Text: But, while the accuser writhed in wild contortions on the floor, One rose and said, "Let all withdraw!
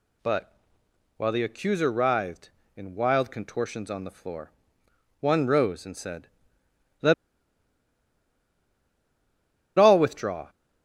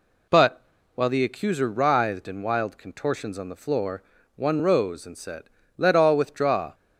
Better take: second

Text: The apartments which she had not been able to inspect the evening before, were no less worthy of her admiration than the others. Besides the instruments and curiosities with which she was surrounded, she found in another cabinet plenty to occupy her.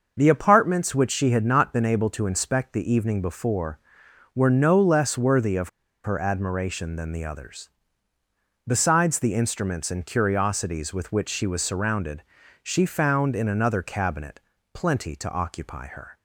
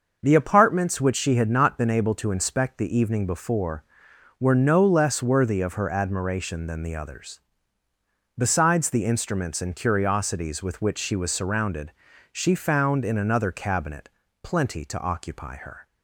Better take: second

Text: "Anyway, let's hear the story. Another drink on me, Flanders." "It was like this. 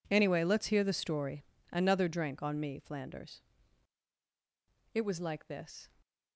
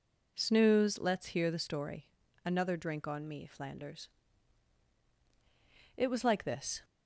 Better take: first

